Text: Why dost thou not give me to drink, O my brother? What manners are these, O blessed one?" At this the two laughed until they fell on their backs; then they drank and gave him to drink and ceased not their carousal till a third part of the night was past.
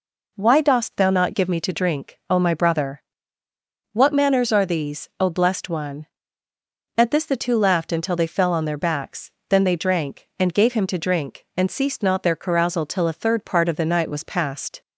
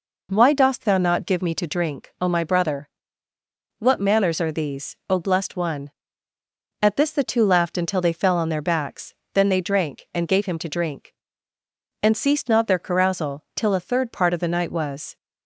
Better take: first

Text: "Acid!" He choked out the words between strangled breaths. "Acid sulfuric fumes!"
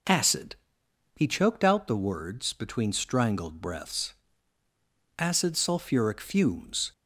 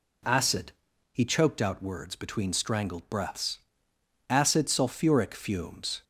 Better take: first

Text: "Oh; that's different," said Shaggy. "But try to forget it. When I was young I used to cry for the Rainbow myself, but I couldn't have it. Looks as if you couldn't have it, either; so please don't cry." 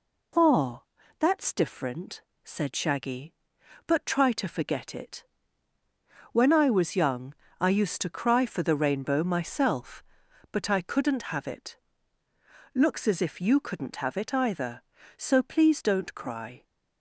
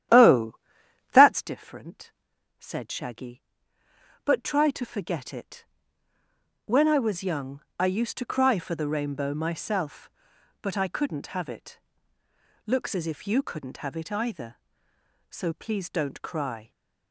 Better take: first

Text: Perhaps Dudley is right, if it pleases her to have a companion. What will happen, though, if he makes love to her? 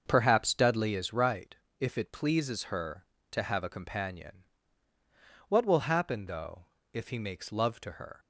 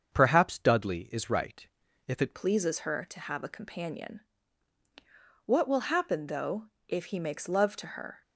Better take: first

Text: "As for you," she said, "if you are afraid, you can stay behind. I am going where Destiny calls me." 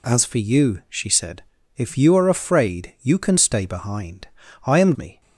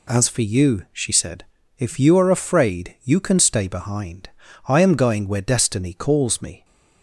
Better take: second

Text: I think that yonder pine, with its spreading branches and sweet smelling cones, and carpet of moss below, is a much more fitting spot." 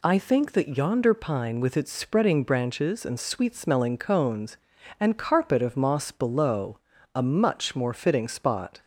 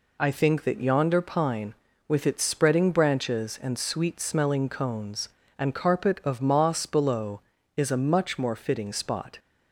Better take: second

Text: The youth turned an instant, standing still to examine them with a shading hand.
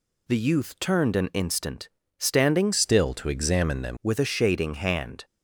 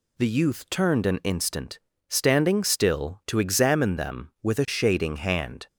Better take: second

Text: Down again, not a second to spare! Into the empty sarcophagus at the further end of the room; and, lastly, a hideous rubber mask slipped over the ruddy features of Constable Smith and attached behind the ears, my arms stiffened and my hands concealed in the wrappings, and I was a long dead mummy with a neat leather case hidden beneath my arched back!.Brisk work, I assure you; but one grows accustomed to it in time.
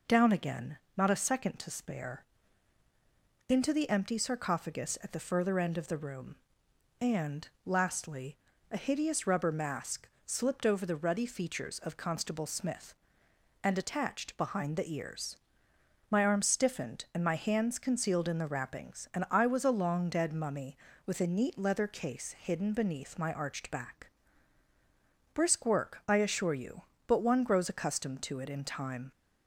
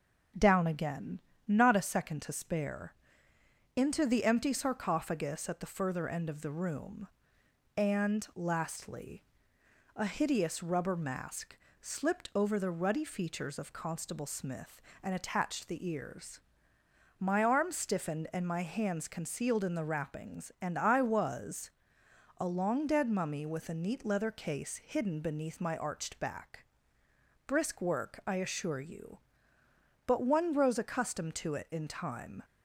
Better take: first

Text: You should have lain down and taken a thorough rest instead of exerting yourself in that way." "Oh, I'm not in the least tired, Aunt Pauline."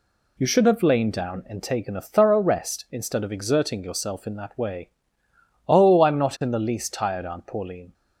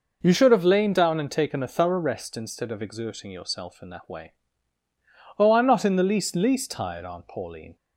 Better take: first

